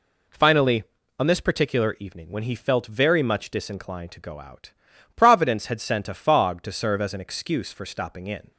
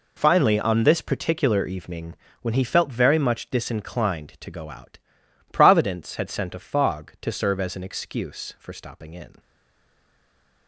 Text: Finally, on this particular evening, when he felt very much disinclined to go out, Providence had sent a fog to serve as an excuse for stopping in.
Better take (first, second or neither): first